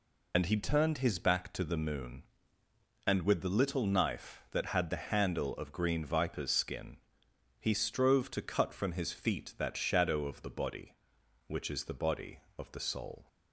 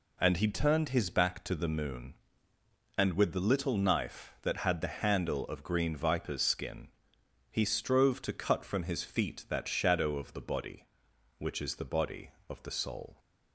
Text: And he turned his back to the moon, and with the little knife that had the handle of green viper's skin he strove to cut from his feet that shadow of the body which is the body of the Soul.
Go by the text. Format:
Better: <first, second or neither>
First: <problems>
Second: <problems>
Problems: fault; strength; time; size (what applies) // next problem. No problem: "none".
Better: second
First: loses the start of "And"; at 0.3 s; 80 ms // pauses between "skin" and "he"; noticeable; at 6.9 s; 0.62 s long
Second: pauses between "skin" and "he"; noticeable; at 6.8 s; 0.62 s long